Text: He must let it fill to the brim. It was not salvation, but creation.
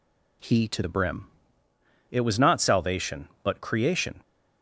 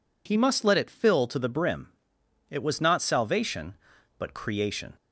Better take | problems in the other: second | skips "must let it fill"; at 0.6 s

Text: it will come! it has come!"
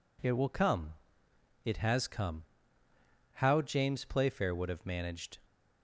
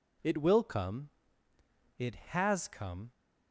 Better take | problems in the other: second | goes on to say "How James Playfair would have managed"; strong; from 3.3 s on; 2.0 s long

